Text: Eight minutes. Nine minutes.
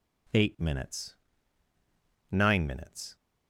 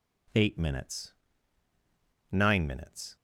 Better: neither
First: none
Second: none

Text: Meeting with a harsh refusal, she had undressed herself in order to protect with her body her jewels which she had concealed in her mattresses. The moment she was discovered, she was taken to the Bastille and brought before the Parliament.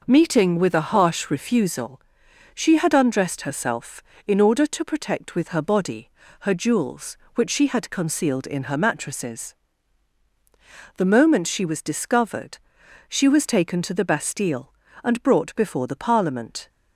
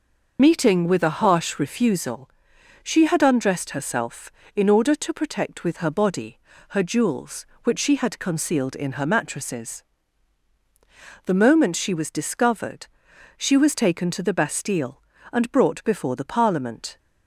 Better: first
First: pauses between "body" and "her"; slight; at 6.1 s; 0.30 s long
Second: loses the start of "Meeting"; at 0.3 s; 90 ms // pauses between "body" and "her"; slight; at 6.3 s; 0.30 s long

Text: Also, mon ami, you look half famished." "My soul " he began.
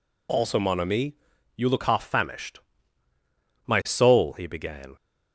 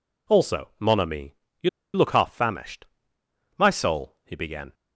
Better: first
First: none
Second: pauses between "you" and "look"; slight; at 1.6 s; 0.26 s long

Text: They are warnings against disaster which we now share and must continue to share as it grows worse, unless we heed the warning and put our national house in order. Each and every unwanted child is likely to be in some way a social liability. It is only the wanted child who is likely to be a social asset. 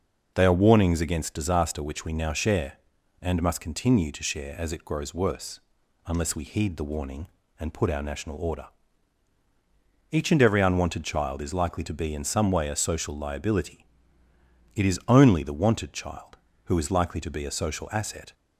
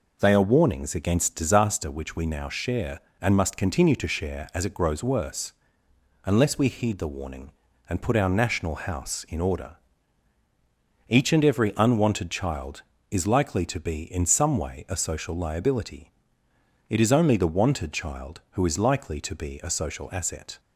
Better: second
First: skips "house in"; at 8.3 s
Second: none

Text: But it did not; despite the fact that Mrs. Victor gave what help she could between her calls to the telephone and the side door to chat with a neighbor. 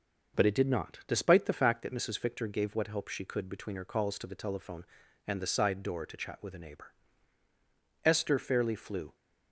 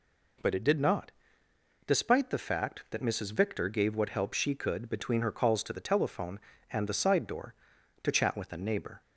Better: second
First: goes on to say "Esther fairly flew"; noticeable; from 8.0 s on; 1.1 s long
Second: none

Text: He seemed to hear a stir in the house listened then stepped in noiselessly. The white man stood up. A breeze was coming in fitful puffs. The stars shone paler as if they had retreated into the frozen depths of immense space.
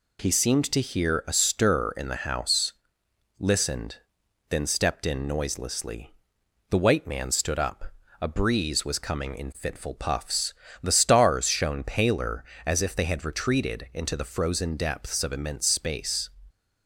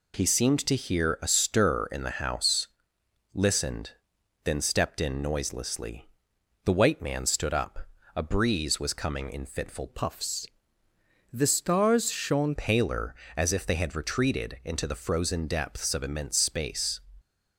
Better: first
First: pauses between "house" and "listened"; noticeable; at 2.7 s; 0.64 s long // pauses between "listened" and "then"; noticeable; at 3.9 s; 0.54 s long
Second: pauses between "house" and "listened"; noticeable; at 2.6 s; 0.64 s long // pauses between "listened" and "then"; noticeable; at 3.9 s; 0.54 s long // changes voice from "puffs" to "shone"; from 9.8 to 12.5 s; 2.7 s long

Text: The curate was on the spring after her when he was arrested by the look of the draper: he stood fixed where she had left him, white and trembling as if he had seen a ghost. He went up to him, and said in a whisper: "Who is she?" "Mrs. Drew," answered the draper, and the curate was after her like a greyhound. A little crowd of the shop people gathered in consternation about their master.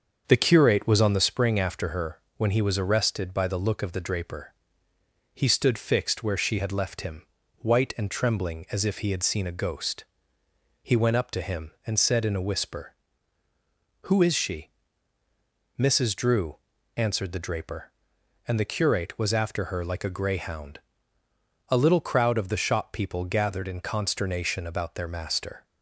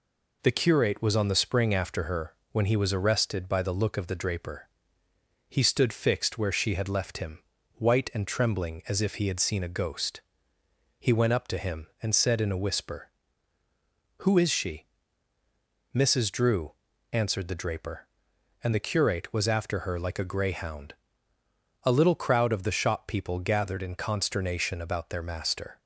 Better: second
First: starts louder than the rest; until 1.2 s; 7 dB // pauses between "her" and "when"; slight; at 2.1 s; 0.20 s long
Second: pauses between "her" and "when"; slight; at 2.3 s; 0.20 s long

